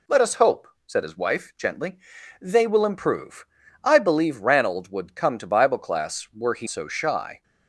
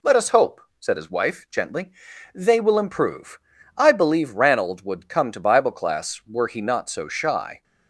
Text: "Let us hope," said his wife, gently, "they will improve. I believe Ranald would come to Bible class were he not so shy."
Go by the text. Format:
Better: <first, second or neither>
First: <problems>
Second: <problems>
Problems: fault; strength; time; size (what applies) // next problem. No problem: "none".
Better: second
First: skips "not"; at 6.6 s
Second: none